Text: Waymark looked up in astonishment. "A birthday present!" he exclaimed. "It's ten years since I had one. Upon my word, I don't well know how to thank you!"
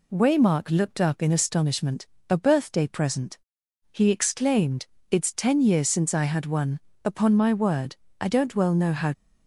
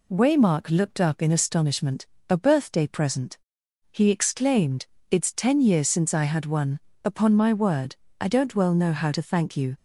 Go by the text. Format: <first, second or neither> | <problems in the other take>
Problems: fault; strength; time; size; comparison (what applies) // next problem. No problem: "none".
second | stops before "to thank you"; at 9.1 s